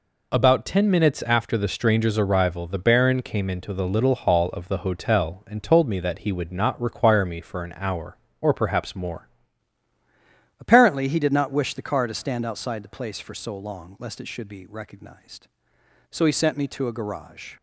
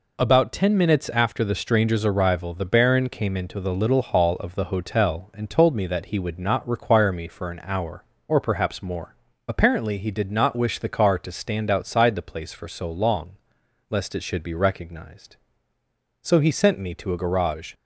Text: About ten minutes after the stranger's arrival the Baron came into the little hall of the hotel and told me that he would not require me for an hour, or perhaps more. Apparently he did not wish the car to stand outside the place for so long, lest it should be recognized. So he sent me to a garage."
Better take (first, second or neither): second